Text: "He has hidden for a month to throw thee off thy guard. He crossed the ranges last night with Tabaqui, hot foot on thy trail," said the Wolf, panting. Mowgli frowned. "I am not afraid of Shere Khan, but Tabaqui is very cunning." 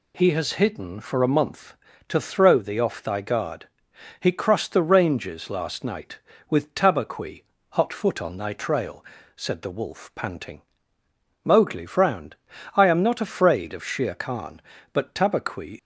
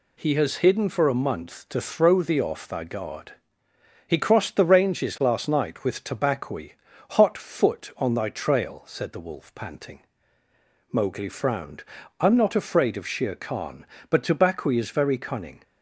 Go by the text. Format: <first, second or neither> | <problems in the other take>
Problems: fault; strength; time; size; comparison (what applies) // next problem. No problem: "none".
second | stops before "is very cunning"; at 15.7 s